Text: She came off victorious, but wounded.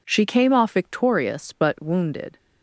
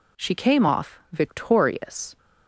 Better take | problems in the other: first | stops before "but wounded"; at 2.1 s

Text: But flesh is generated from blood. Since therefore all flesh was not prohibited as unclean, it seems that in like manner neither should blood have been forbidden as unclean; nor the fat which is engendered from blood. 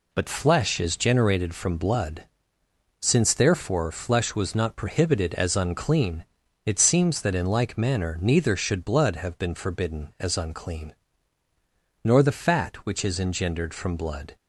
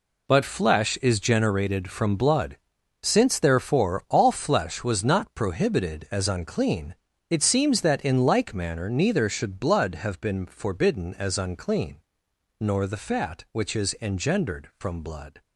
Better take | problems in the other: second | skips "all"; at 3.9 s

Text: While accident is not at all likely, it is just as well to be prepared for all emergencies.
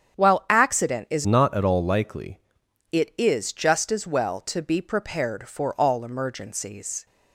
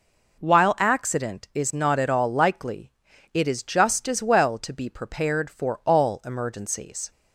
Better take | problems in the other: second | starts louder than the rest; strong; until 1.2 s; 8.5 dB // changes voice from "not" to "likely"; from 1.2 to 2.3 s; 1.1 s long

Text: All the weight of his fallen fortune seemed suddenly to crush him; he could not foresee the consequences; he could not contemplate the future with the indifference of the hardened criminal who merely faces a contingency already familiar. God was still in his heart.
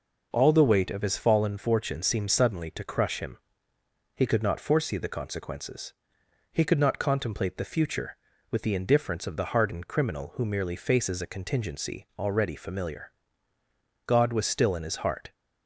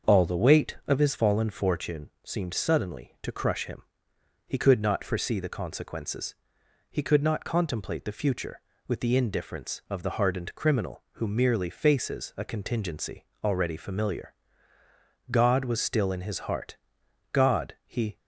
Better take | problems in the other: first | starts louder than the rest; until 1.1 s; 6.5 dB // pauses between "fortune" and "seemed"; slight; at 2.0 s; 0.16 s long // pauses between "contingency" and "already"; slight; at 13.2 s; 0.18 s long // goes on to say "God he"; noticeable; from 17.3 s on; 0.86 s long

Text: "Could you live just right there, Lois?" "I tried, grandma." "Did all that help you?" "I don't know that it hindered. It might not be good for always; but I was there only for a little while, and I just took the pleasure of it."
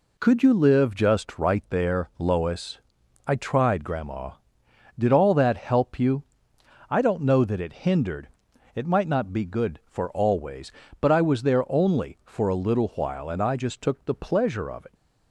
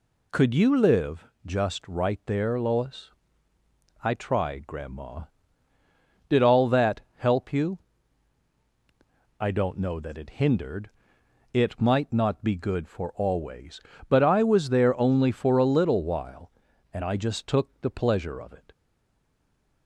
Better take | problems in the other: first | pauses between "live" and "just"; slight; at 1.2 s; 0.20 s long // pauses between "that" and "help"; slight; at 7.0 s; 0.16 s long // stays silent after the last word; from 18.7 s on; 1.1 s long

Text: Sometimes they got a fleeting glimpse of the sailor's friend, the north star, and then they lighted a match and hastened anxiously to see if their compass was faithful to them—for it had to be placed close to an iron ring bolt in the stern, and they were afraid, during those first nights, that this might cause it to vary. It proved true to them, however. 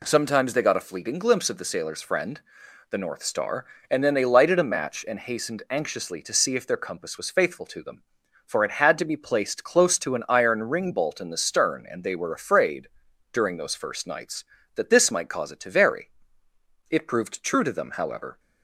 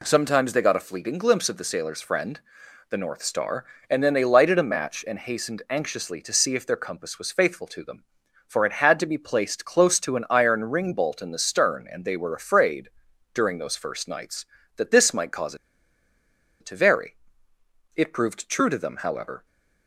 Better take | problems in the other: first | pauses between "cause" and "it"; at 15.5 s; 1.0 s long

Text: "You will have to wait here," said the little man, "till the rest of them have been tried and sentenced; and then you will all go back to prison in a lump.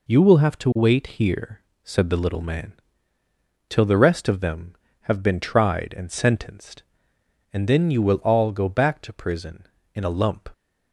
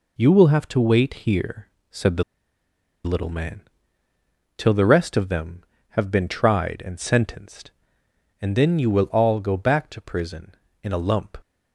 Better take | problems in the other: first | pauses between "wait" and "here"; slight; at 1.1 s; 0.16 s long; slight in the first // pauses between "the" and "little"; noticeable; at 2.2 s; 0.82 s long

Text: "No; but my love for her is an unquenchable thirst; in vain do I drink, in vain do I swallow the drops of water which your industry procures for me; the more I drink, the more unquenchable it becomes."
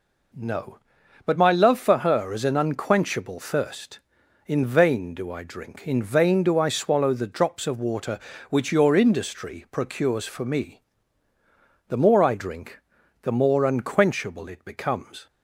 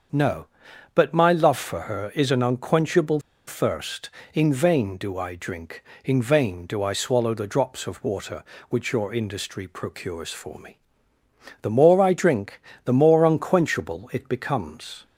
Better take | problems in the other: first | starts louder than the rest; until 1.6 s; 7 dB // pauses between "unquenchable" and "thirst"; slight; at 3.1 s; 0.27 s long

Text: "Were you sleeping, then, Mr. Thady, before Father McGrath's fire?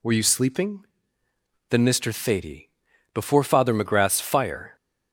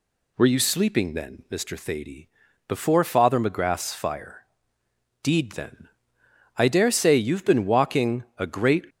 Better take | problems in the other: first | goes on to say "deed then I dare say you've been walking a great"; strong; from 5.2 s on; 3.6 s long

